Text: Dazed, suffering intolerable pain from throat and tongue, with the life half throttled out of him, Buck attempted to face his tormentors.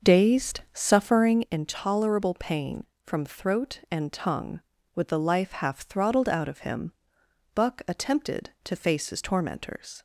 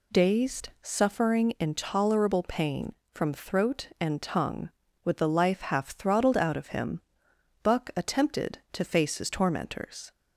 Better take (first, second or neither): second